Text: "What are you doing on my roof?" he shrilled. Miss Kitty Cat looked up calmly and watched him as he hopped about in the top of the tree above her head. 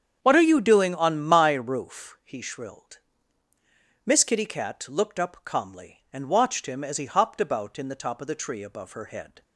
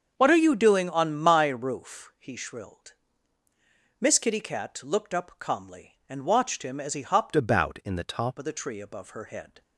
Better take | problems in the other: first | starts louder than the rest; until 1.1 s; 7 dB; strong in the first // changes voice from "about" to "top"; from 7.3 to 8.3 s; 1.0 s long

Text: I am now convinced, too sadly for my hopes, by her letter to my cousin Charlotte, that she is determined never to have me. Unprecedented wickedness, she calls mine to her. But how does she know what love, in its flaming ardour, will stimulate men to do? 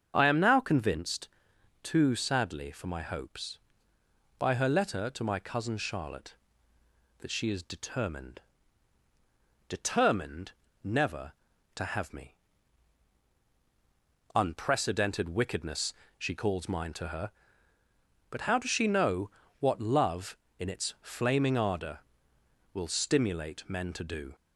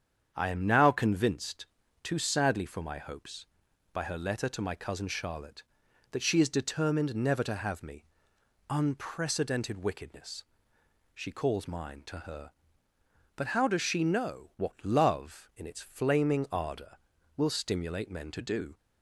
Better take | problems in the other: second | starts louder than the rest; strong; until 1.1 s; 7.5 dB; strong in the second // says "determined" twice; at 9.6 s // pauses between "know" and "what"; slight; at 19.3 s; 0.28 s long

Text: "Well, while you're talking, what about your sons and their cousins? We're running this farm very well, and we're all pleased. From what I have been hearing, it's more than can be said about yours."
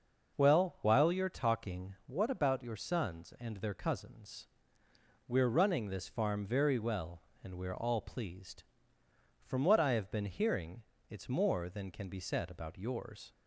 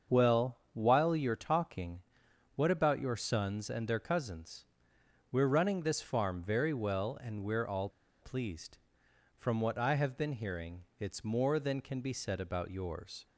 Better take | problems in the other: first | starts louder than the rest; until 1.2 s; 6.5 dB // pauses between "all" and "pleased"; slight; at 7.8 s; 0.33 s long

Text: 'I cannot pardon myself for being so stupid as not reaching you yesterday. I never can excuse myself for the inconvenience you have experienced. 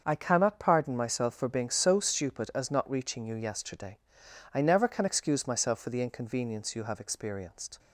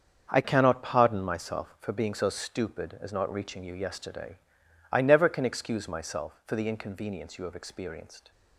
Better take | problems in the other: first | starts louder than the rest; until 1.3 s; 7 dB; also in the first // changes voice at "cannot"; from 0.4 s on; 7.9 s long

